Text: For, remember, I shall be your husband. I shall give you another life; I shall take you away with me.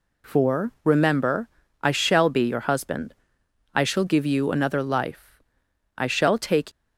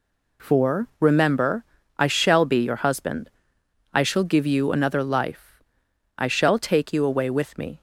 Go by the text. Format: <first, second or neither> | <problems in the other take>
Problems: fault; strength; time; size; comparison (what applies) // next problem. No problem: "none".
second | stops before "you away with me"; at 6.7 s